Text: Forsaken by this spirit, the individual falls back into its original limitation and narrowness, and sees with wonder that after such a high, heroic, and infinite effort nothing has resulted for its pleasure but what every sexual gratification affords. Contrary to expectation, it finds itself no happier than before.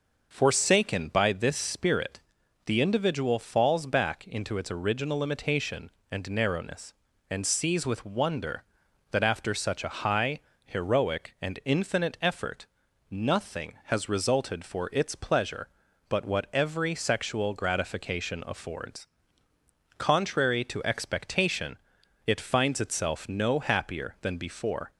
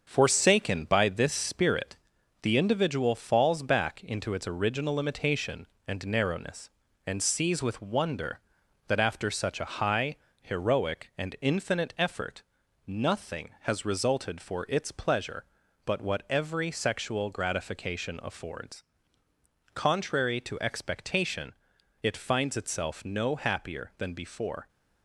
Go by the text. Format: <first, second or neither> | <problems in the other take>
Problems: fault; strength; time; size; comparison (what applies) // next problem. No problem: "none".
first | gets quieter; noticeable; throughout; 5 dB // pauses between "effort" and "nothing"; at 12.4 s; 0.44 s long; also in the first